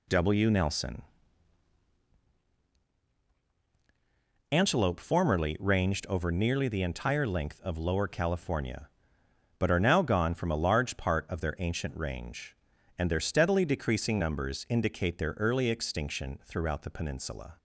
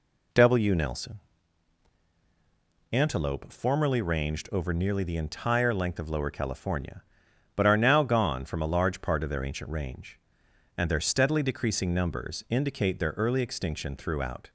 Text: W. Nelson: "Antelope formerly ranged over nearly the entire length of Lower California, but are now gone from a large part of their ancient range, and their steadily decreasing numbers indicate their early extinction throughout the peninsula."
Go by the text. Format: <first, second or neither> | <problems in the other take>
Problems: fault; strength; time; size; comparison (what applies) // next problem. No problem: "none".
first | stops before "the peninsula"; at 14.4 s